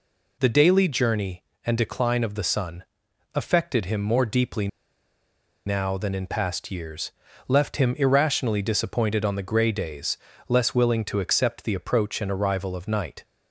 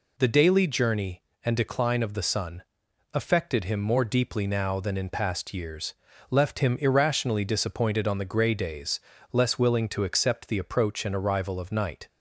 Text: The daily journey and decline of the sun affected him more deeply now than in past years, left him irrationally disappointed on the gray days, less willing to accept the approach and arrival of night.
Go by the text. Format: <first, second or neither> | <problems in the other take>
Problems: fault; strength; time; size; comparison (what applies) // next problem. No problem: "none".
second | pauses between "sun" and "affected"; noticeable; at 2.8 s; 0.50 s long; noticeable in the second // pauses between "deeply" and "now"; at 4.6 s; 0.98 s long